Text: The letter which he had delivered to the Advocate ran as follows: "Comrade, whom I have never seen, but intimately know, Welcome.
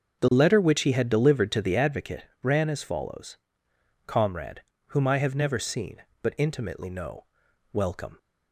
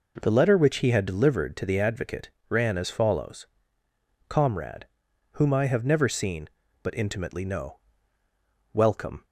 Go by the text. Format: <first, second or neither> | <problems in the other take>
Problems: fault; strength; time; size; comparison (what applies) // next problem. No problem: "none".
second | starts louder than the rest; until 2.0 s; 6 dB // pauses between "Advocate" and "ran"; slight; at 2.2 s; 0.18 s long; slight in the second